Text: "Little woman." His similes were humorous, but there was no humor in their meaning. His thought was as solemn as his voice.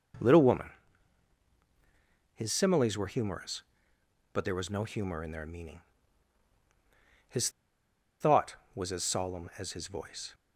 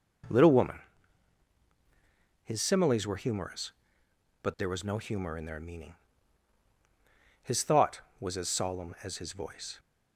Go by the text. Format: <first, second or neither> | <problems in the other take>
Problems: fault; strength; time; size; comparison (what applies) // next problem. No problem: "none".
second | pauses between "His" and "thought"; noticeable; at 7.4 s; 0.71 s long